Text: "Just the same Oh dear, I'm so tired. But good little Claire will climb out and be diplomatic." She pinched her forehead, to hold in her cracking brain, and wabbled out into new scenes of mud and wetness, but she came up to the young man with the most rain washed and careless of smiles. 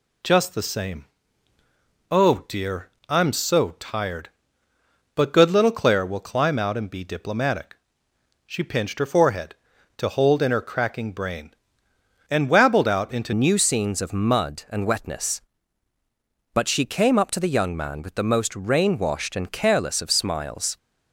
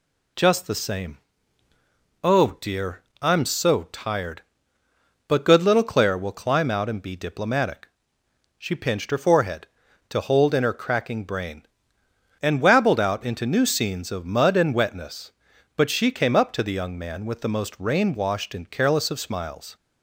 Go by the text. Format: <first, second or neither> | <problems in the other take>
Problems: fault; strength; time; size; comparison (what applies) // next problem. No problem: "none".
second | pauses between "same" and "Oh"; at 1.0 s; 1.0 s long; also in the second // changes voice at "new"; from 13.3 s on; 7.4 s long